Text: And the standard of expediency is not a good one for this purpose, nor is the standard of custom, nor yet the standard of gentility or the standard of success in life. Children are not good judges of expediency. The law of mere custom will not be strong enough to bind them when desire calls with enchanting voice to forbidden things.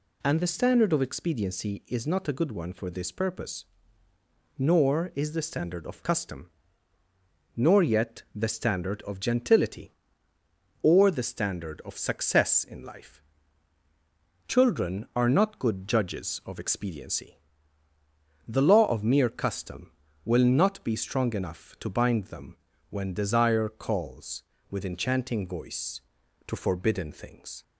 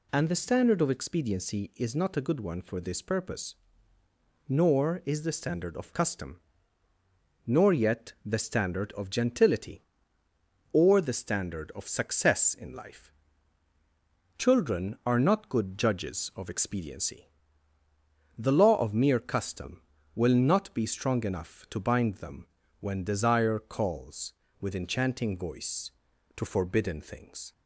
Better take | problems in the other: neither | pauses between "them" and "when"; slight; the same in both

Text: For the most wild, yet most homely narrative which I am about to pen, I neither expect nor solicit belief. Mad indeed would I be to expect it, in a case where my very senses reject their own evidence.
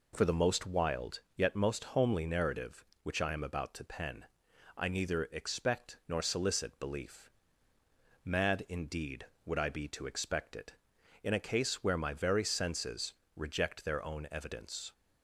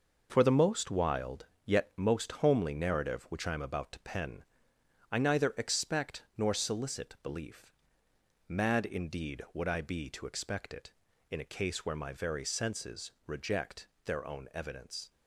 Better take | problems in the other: first | gets quieter; throughout; 7 dB // pauses between "senses" and "reject"; slight; at 13.1 s; 0.16 s long; slight in the first // pauses between "reject" and "their"; slight; at 13.8 s; 0.16 s long

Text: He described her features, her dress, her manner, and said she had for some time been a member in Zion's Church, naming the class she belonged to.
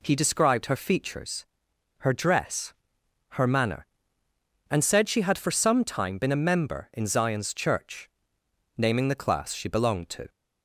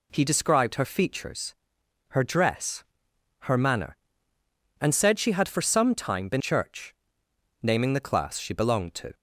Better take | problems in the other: first | skips "a member in Zion's"; at 6.4 s

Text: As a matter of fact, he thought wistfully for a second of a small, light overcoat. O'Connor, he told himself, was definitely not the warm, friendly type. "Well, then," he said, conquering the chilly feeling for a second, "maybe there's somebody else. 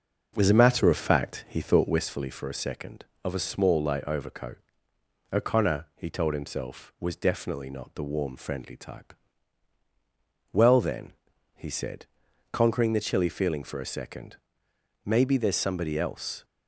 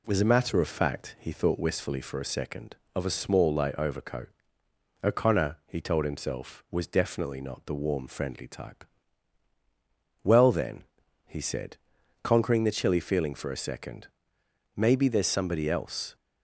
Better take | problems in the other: second | starts louder than the rest; noticeable; until 2.1 s; 5.5 dB

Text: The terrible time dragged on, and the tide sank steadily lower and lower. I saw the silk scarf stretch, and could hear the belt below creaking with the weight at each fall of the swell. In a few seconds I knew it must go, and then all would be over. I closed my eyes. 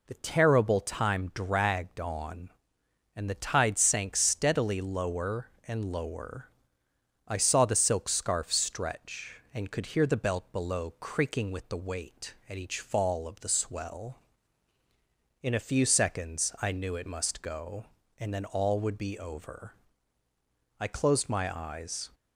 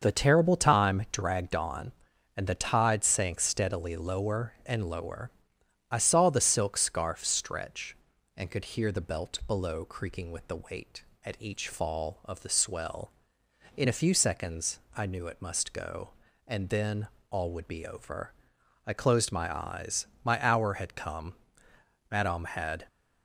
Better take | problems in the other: first | starts louder than the rest; until 1.0 s; 6.5 dB // pauses between "seconds" and "I"; slight; at 14.7 s; 0.16 s long // pauses between "then" and "all"; slight; at 17.0 s; 0.20 s long // goes on to say "My hour had come Madame had"; strong; from 20.2 s on; 2.6 s long

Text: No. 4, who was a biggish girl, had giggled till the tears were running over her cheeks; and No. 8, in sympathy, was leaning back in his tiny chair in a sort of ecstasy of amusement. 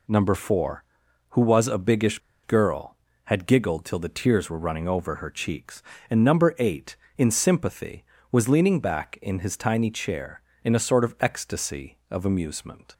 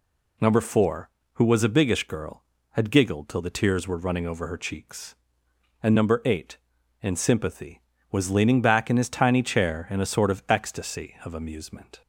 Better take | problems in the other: second | pauses between "biggish" and "girl"; slight; at 2.1 s; 0.25 s long

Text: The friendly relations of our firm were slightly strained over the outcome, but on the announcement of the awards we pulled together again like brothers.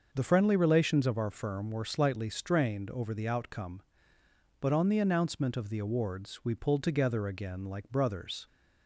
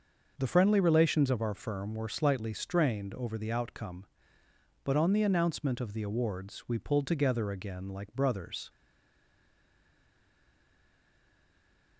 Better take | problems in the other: first | starts louder than the rest; noticeable; until 1.3 s; 6 dB; noticeable in the first // stays silent after the last word; strong; from 8.6 s on; 3.3 s long

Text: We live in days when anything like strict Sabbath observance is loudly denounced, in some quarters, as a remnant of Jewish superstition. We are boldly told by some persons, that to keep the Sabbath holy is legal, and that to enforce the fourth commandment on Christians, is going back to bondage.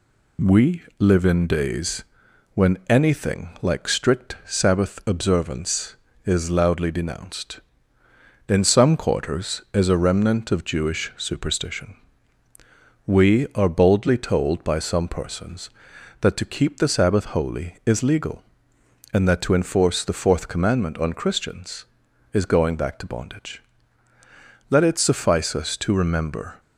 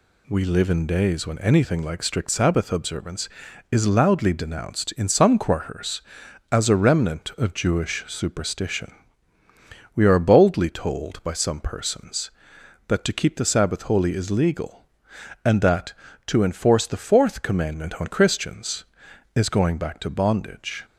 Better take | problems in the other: second | pauses between "We" and "live"; slight; at 0.8 s; 0.16 s long // pauses between "days" and "when"; noticeable; at 2.0 s; 0.50 s long // goes on to say "Let it suffice us to remember"; strong; from 24.6 s on; 1.9 s long

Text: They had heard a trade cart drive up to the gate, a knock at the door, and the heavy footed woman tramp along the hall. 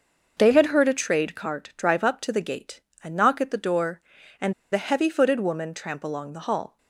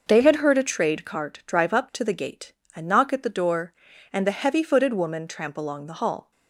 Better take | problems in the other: second | pauses between "and" and "the"; slight; at 4.5 s; 0.19 s long

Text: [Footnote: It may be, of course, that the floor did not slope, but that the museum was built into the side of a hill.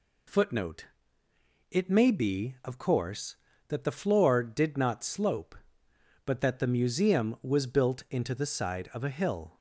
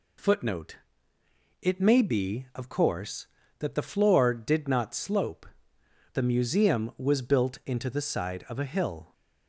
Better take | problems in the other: first | skips "but that"; at 5.7 s

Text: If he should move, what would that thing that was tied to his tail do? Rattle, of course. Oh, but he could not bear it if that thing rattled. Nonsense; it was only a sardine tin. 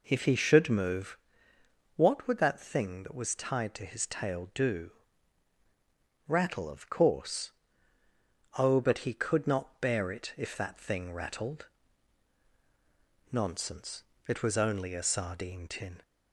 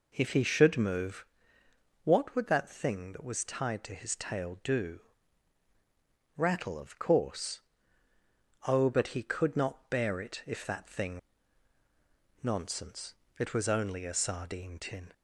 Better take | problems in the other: first | skips "rattled"; at 11.8 s

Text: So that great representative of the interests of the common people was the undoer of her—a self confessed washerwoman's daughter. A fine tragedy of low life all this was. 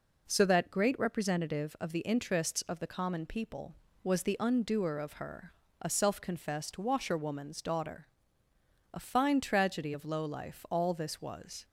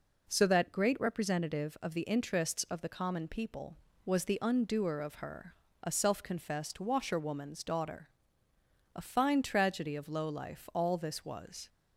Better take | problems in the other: neither | none

